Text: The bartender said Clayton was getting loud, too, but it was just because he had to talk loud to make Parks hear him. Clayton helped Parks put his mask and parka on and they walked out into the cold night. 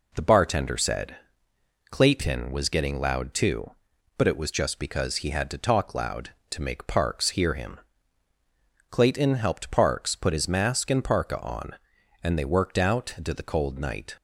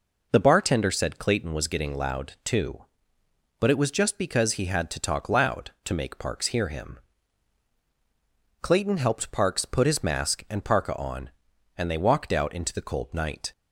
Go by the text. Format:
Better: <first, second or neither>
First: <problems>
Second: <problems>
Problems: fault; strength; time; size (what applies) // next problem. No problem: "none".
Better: second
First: pauses between "said" and "Clayton"; noticeable; at 1.1 s; 0.74 s long // says "worked" for "walked"; at 12.4 s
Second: none